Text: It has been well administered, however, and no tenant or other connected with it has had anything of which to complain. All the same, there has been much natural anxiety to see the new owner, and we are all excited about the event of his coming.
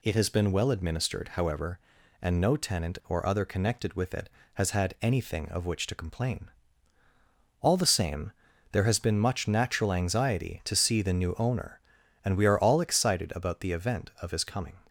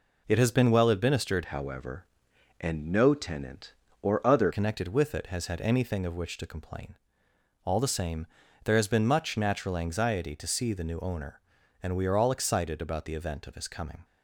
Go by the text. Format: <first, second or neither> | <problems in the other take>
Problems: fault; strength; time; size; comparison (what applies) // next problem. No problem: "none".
first | changes voice from "however" to "other"; from 1.4 to 4.5 s; 3.1 s long